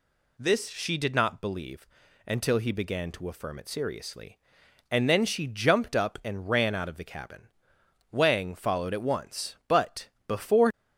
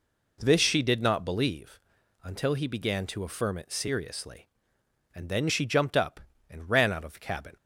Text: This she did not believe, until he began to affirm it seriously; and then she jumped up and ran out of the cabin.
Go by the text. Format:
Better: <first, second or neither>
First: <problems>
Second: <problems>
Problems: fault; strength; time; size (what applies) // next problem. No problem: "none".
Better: second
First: goes on to say "Wang followed at once but before"; strong; from 8.0 s on; 2.6 s long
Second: none